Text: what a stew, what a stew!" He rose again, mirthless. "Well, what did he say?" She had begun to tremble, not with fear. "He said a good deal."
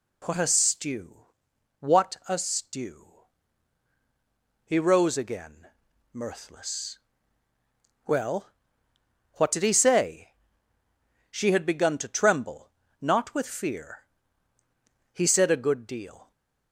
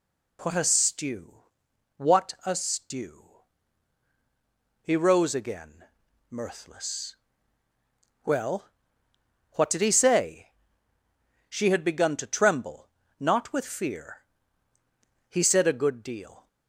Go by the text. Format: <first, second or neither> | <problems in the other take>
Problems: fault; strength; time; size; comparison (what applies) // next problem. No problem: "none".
neither | none